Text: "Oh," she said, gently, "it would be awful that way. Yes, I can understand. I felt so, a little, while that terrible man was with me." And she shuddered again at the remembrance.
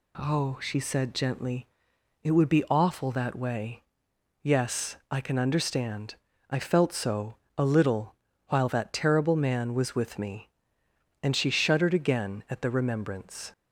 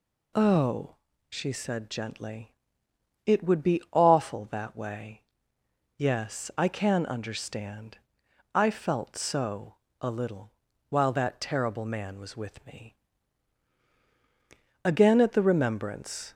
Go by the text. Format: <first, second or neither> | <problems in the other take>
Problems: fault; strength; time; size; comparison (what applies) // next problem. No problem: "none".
first | skips "And she shuddered"; at 13.8 s